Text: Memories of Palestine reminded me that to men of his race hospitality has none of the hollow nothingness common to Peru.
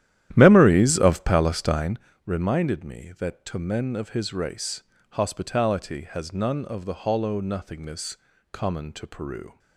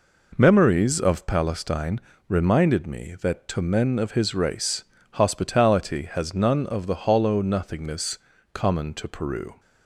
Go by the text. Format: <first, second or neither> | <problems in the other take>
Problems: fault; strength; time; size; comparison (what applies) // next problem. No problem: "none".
second | starts louder than the rest; strong; until 2.0 s; 12 dB // pauses between "Palestine" and "reminded"; slight; at 1.9 s; 0.25 s long; slight in the second // pauses between "race" and "hospitality"; slight; at 4.8 s; 0.32 s long; slight in the second // pauses between "nothingness" and "common"; slight; at 8.1 s; 0.36 s long; slight in the second